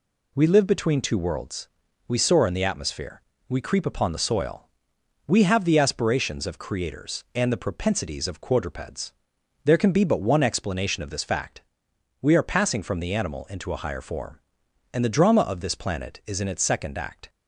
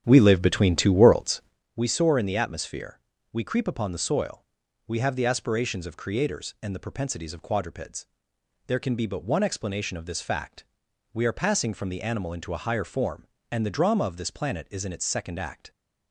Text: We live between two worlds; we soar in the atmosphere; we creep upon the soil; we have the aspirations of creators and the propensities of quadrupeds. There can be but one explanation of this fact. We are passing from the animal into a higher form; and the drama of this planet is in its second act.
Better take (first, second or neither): first